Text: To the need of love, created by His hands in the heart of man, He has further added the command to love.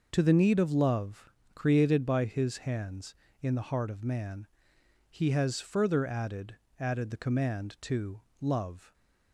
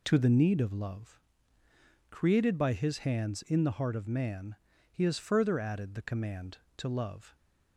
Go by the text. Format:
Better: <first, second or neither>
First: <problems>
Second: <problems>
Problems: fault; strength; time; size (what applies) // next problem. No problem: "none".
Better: second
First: says "added" twice; at 6.7 s // pauses between "to" and "love"; slight; at 8.2 s; 0.18 s long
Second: none